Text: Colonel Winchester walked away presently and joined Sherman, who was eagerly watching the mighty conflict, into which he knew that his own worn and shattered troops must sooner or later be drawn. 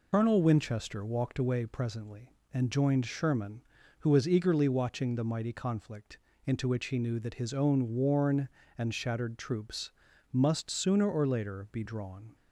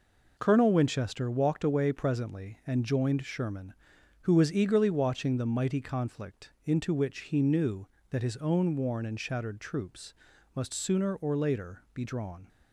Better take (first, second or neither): second